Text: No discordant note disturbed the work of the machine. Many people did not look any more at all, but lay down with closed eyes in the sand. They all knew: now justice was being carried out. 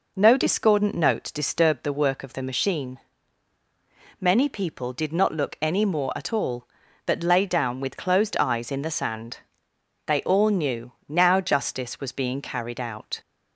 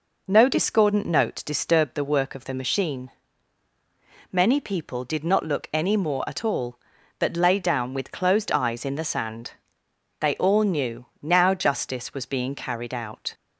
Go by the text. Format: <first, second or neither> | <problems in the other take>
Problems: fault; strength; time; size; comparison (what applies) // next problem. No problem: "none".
neither | none